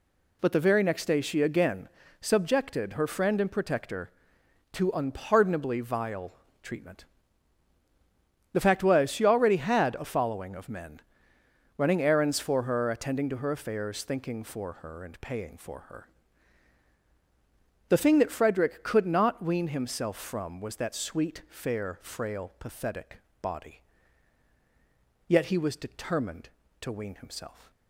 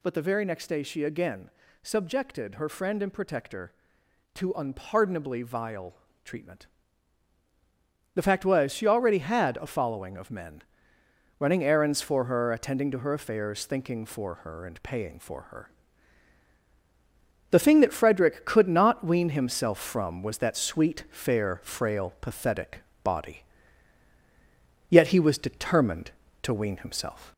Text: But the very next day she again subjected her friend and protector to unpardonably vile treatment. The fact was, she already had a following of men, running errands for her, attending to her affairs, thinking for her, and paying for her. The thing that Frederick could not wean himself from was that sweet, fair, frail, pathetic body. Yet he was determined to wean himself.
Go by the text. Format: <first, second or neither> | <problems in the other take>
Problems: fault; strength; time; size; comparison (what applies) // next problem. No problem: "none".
first | gets louder; slight; throughout; 2.5 dB // pauses between "again" and "subjected"; slight; at 1.4 s; 0.32 s long; slight in the first // pauses between "vile" and "treatment"; slight; at 5.9 s; 0.30 s long; slight in the first // pauses between "pathetic" and "body"; slight; at 22.7 s; 0.24 s long; slight in the first